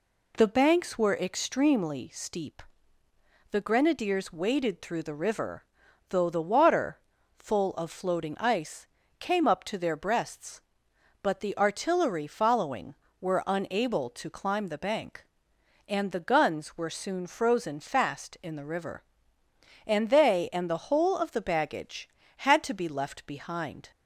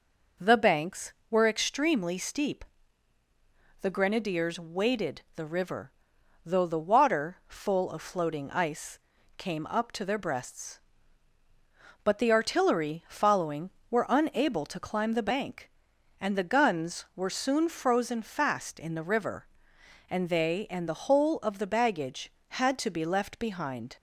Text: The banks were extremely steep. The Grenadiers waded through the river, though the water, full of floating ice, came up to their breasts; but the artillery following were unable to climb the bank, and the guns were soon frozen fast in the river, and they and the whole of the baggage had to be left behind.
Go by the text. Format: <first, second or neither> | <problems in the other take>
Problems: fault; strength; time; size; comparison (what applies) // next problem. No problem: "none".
first | skips "through"; at 5.2 s